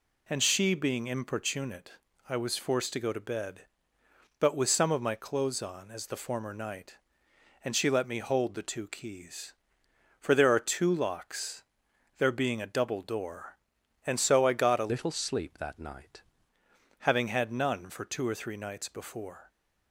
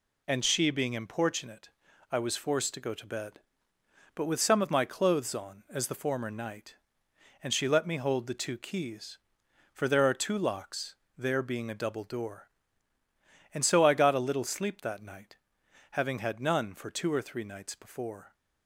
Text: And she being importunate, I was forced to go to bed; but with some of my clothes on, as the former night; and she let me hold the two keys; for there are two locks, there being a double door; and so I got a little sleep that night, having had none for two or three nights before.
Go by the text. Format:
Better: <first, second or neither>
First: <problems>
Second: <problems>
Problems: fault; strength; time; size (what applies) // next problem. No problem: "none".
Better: second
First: changes voice from "little" to "night"; from 14.9 to 16.2 s; 1.3 s long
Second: none